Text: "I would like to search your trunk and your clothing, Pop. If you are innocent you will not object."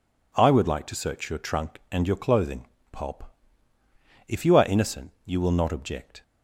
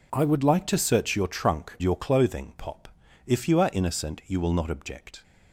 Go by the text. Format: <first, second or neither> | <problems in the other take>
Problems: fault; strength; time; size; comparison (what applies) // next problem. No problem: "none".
first | skips "and"; at 1.8 s